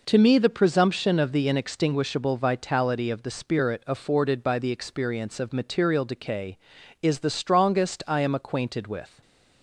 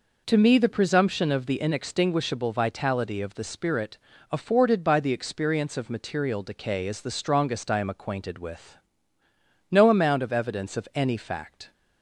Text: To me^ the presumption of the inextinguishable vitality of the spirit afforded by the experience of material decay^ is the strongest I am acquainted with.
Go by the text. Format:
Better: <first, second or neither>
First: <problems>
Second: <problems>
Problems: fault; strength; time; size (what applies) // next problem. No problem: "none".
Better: first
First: none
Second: pauses between "spirit" and "afforded"; slight; at 3.9 s; 0.32 s long // goes on to say "No amount of evidence of any fact"; strong; from 9.7 s on; 2.0 s long